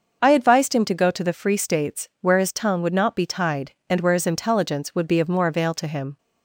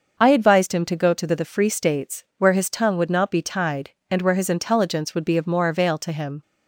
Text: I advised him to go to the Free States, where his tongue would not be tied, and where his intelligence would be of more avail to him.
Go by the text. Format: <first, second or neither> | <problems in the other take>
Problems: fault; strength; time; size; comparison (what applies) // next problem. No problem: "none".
first | starts louder than the rest; until 1.2 s; 6.5 dB; also in the first // says "the" twice; at 1.3 s